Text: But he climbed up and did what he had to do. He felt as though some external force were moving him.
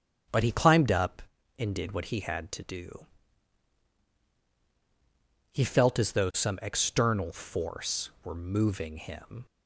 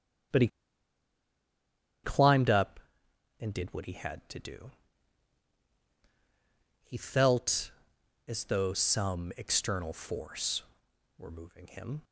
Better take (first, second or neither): first